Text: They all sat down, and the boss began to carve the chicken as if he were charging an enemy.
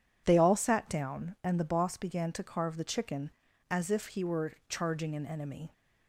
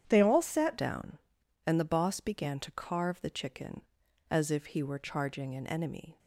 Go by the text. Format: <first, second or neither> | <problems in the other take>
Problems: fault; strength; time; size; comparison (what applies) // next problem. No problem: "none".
first | starts louder than the rest; strong; until 1.0 s; 9 dB // changes voice at "down"; from 0.7 s on; 5.4 s long